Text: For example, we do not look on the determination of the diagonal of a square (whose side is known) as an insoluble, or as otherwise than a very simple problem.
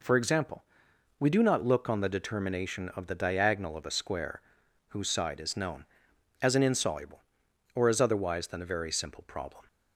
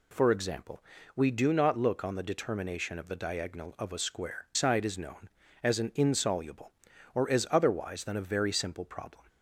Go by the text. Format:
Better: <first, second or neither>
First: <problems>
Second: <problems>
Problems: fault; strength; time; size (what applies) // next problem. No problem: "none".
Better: first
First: none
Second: skips "whose"; at 4.5 s